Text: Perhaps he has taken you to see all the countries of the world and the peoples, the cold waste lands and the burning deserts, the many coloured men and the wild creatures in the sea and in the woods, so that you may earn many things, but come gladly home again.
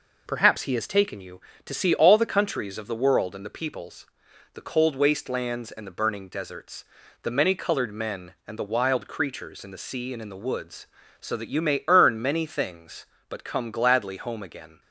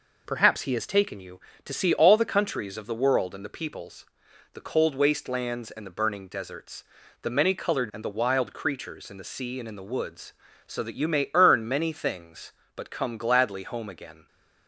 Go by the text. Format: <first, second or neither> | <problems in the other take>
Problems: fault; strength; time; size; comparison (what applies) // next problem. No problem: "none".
first | skips "men"; at 7.9 s